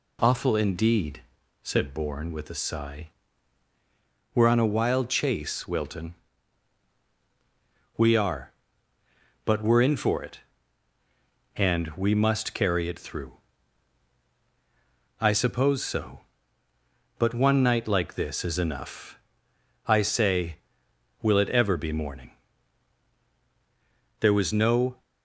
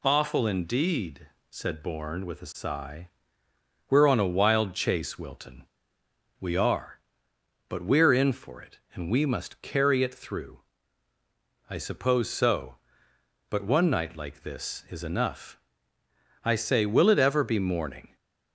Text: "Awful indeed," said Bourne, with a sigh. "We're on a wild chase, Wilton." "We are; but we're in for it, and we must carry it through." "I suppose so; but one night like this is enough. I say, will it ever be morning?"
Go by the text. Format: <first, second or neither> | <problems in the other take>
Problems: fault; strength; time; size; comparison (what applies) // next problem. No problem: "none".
second | goes on to say "There was no"; noticeable; from 24.1 s on; 0.82 s long